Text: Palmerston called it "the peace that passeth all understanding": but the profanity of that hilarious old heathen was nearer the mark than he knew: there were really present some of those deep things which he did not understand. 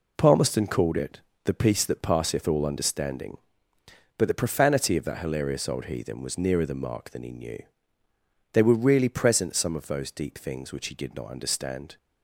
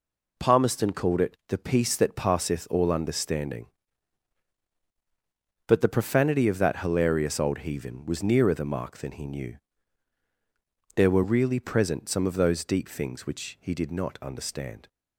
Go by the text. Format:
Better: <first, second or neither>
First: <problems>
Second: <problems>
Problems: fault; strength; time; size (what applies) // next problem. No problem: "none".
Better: second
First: pauses between "it" and "the"; slight; at 1.1 s; 0.24 s long // says "they" for "there"; at 8.5 s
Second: none